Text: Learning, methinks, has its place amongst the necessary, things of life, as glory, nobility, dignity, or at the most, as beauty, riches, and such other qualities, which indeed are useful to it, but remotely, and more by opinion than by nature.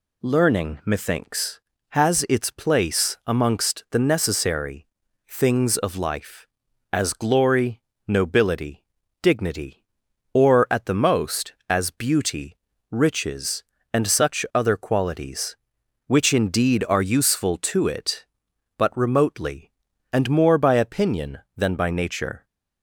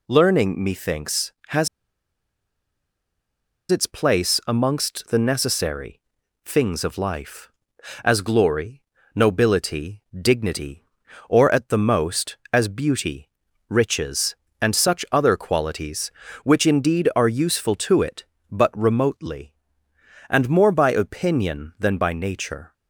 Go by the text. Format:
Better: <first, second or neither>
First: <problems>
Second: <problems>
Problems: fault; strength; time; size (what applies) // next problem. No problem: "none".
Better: first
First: none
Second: pauses between "has" and "its"; strong; at 1.6 s; 2.0 s long